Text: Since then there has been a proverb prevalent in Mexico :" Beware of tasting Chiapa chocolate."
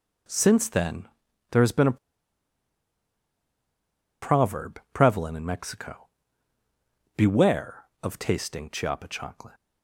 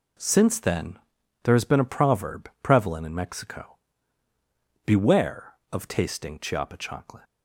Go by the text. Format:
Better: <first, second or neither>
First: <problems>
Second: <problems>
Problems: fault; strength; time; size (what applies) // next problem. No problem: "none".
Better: second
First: pauses between "then" and "there"; at 1.0 s; 0.44 s long // pauses between "a" and "proverb"; strong; at 1.9 s; 2.2 s long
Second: pauses between "then" and "there"; noticeable; at 0.9 s; 0.45 s long